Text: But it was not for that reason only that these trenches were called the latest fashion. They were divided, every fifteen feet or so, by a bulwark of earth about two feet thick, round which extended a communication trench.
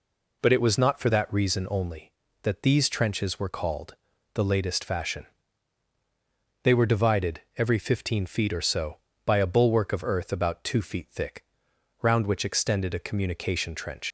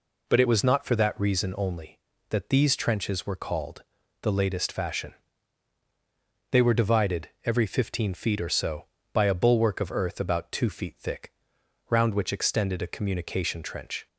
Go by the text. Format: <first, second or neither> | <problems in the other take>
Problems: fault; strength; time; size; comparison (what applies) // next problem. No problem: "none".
second | pauses between "called" and "the"; at 3.9 s; 0.40 s long; also in the second // leaves "trench" unfinished; at 14.0 s; 90 ms